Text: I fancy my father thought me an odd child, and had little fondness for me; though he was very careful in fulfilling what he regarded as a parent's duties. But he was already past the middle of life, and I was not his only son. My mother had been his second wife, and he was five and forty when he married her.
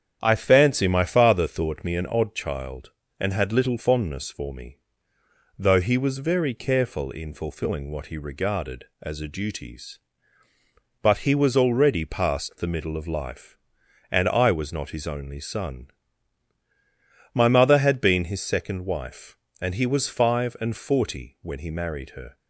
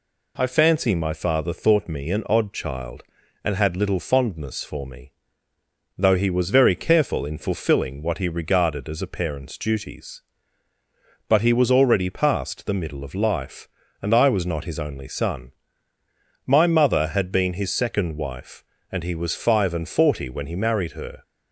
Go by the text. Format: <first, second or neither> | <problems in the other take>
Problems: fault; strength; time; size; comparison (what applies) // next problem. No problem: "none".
second | starts louder than the rest; strong; until 1.2 s; 8.5 dB // skips "parent's"; at 9.2 s